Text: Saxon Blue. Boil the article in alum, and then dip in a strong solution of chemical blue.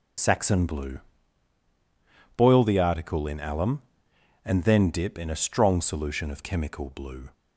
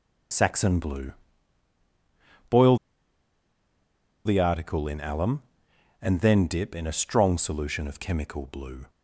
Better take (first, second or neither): first